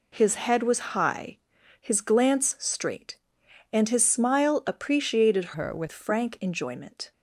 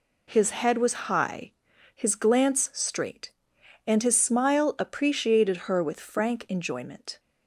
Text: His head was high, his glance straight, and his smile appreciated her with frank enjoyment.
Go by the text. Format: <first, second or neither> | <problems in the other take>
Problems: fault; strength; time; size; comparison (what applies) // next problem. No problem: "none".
second | changes voice from "her" to "with"; from 5.5 to 5.9 s; 0.4 s long